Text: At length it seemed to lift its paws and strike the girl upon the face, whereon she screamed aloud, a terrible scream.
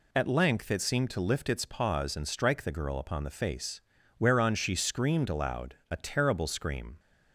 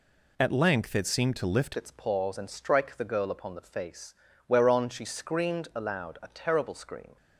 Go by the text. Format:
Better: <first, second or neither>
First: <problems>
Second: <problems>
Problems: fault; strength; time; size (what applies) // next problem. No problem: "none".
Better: first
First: none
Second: changes voice at "its"; from 1.7 s on; 5.4 s long